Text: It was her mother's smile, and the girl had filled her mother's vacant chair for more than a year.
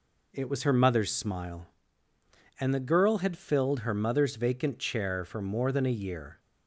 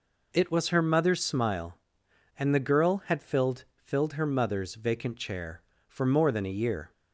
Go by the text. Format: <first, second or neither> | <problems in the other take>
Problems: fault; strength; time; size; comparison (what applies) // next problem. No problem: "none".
first | says "filled" twice; at 3.7 s